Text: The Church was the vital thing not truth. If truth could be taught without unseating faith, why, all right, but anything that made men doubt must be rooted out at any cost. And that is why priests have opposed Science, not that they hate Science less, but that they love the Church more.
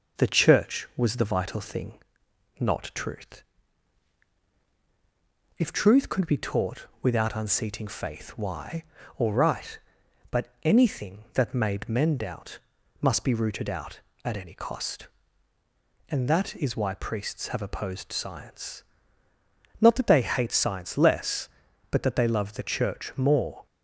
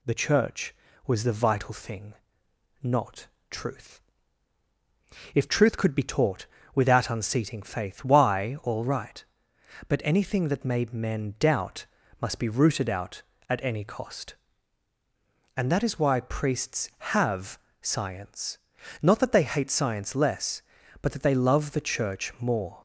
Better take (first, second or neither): first